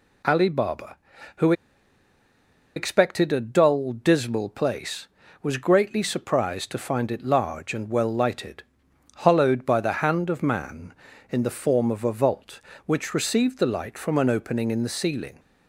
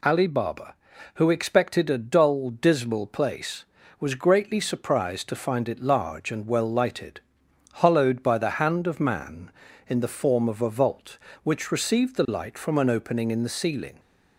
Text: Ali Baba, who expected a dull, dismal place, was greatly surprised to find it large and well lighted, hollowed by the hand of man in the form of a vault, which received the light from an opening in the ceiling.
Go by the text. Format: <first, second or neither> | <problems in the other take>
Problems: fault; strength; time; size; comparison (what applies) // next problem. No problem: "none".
second | pauses between "who" and "expected"; at 1.5 s; 1.2 s long